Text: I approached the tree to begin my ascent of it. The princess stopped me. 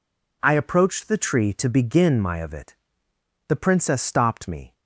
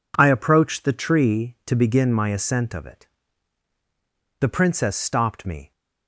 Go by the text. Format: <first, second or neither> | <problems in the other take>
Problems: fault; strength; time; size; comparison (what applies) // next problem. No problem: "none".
second | skips "ascent"; at 2.3 s